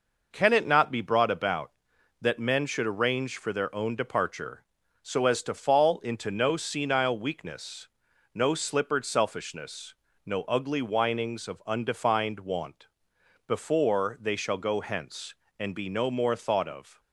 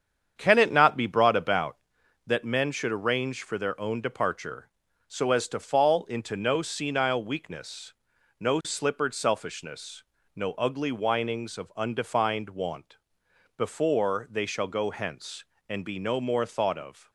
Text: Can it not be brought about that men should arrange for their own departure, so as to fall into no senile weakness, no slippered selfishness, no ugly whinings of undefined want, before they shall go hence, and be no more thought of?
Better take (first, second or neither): first